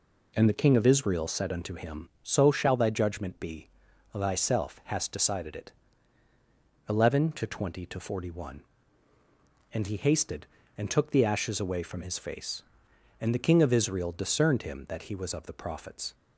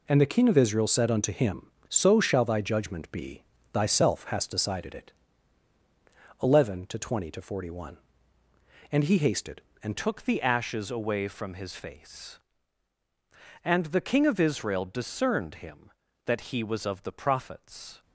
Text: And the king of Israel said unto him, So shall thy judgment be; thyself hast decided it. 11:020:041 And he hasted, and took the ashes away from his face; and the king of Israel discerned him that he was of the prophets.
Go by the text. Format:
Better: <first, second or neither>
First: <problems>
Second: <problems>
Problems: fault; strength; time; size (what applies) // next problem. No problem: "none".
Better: first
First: none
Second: changes voice at "took"; from 9.9 s on; 8.1 s long